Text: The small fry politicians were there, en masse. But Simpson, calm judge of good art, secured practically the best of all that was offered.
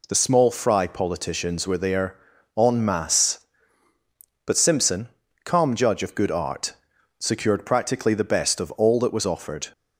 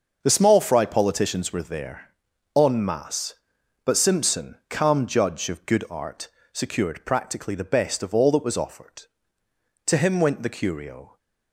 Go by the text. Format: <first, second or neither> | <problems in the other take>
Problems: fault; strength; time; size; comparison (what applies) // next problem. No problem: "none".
first | starts louder than the rest; until 1.2 s; 6 dB // goes on to say "To him went the curio"; noticeable; from 9.8 s on; 1.3 s long